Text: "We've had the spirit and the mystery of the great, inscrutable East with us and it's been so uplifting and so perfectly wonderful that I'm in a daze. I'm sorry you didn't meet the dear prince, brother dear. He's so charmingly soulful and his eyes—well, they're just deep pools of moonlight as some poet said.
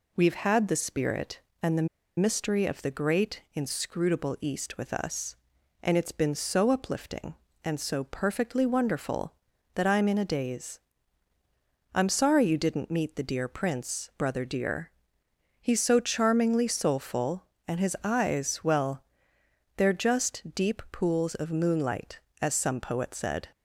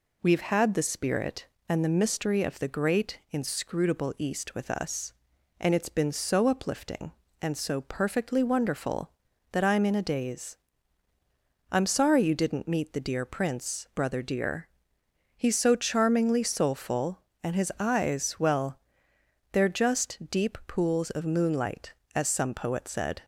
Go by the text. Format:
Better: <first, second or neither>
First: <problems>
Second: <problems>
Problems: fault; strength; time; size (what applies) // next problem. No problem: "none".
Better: second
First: pauses between "the" and "mystery"; slight; at 1.8 s; 0.32 s long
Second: none